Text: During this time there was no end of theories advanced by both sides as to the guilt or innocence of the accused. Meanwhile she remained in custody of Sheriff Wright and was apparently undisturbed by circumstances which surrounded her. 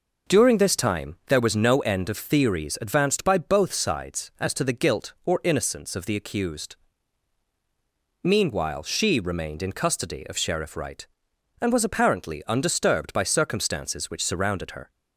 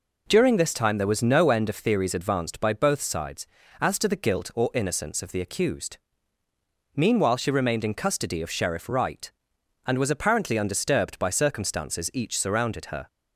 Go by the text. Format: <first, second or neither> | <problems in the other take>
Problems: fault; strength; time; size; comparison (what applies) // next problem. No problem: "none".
first | says "each" for "which"; at 12.1 s